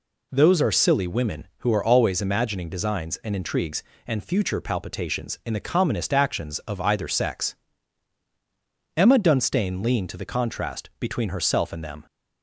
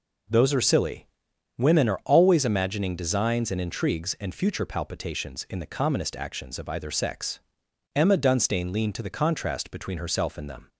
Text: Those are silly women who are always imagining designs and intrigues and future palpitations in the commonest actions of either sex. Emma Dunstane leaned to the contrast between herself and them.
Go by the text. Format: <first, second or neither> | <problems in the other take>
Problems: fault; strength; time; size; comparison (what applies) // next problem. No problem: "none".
first | pauses between "silly" and "women"; noticeable; at 1.0 s; 0.50 s long // skips "who"; at 1.8 s